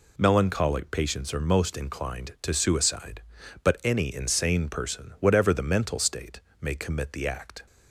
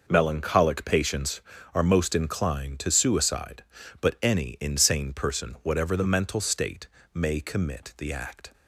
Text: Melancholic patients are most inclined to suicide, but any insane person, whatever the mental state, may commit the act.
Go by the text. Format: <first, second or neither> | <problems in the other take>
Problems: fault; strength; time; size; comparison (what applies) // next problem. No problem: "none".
neither | none